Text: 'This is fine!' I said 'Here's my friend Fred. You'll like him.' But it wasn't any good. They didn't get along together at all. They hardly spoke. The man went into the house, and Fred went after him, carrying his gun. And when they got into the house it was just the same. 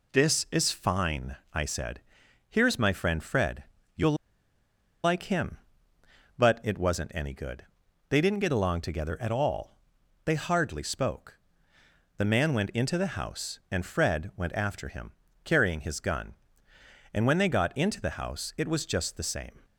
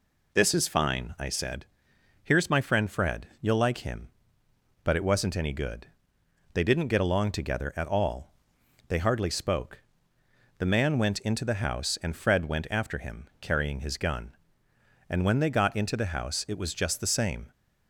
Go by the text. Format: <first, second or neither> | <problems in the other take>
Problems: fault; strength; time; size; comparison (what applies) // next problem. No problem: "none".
second | pauses between "said" and "Here's"; noticeable; at 2.0 s; 0.48 s long; noticeable in the second // pauses between "You'll" and "like"; noticeable; at 4.1 s; 0.89 s long